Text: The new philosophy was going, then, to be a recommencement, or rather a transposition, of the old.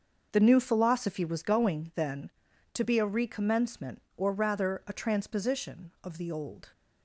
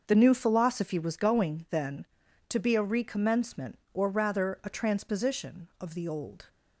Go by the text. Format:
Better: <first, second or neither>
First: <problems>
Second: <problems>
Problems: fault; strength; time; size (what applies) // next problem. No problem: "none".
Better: neither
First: starts louder than the rest; until 1.3 s; 6 dB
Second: starts louder than the rest; until 1.0 s; 6 dB